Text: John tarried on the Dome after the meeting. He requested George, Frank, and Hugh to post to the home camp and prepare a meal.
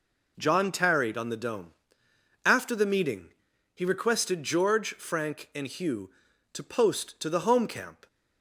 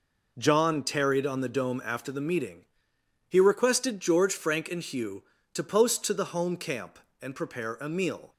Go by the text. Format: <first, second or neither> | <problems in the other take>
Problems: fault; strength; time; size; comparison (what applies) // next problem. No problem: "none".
second | pauses between "Dome" and "after"; noticeable; at 1.7 s; 0.74 s long // stops before "and prepare a meal"; at 8.0 s